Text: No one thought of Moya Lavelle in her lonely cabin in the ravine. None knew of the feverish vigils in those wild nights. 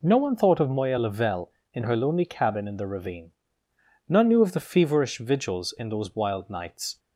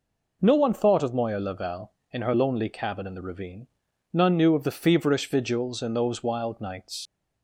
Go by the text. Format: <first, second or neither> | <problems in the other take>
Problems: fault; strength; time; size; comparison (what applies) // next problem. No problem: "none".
first | leaves "nights" unfinished; at 7.0 s; 50 ms